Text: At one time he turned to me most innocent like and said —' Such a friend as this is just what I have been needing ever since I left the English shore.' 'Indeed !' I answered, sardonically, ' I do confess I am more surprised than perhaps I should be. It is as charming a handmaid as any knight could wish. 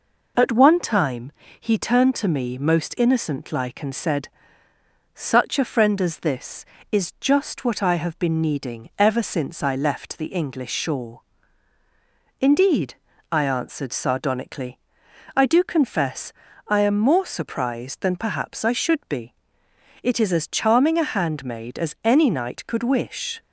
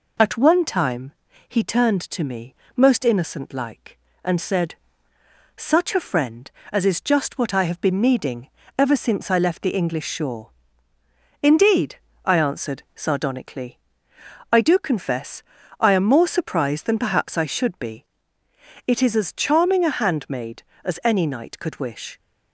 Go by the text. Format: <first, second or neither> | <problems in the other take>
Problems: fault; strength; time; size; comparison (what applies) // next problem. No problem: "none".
first | pauses between "time" and "he"; slight; at 1.1 s; 0.36 s long; slight in the first // pauses between "me" and "most"; slight; at 2.5 s; 0.18 s long // skips "this"; at 6.8 s // pauses between "needing" and "ever"; slight; at 8.4 s; 0.30 s long // pauses between "confess" and "I"; slight; at 15.4 s; 0.36 s long; slight in the first